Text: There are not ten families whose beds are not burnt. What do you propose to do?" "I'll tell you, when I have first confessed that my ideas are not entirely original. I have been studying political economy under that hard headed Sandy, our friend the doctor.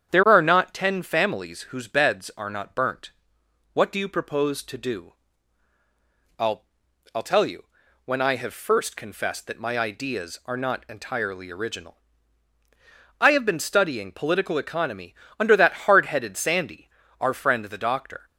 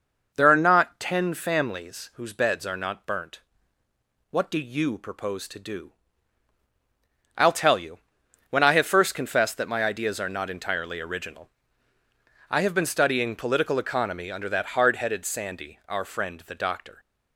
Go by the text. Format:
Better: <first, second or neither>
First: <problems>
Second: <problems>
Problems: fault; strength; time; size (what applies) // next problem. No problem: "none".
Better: second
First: starts louder than the rest; strong; until 1.1 s; 8.5 dB // says "I'll" twice; at 7.1 s // pauses between "economy" and "under"; slight; at 15.1 s; 0.28 s long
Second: none